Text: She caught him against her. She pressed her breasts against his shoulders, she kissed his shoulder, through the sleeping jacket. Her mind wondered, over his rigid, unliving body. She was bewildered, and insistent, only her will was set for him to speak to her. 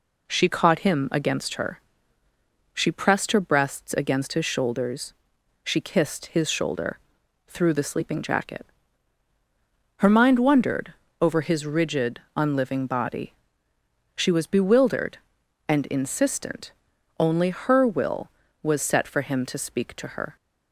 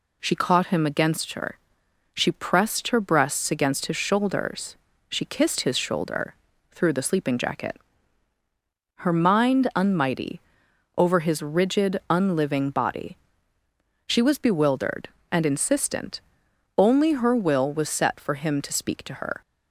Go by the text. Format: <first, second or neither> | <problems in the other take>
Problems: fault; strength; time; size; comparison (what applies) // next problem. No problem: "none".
first | says "unmighty" for "wondered"; at 9.7 s